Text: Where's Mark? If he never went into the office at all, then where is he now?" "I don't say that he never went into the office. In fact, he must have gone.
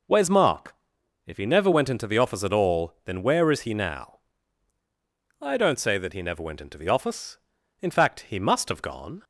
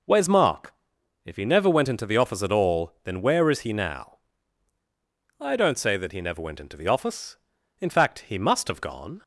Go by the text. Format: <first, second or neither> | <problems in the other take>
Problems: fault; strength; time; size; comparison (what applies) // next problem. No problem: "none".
neither | none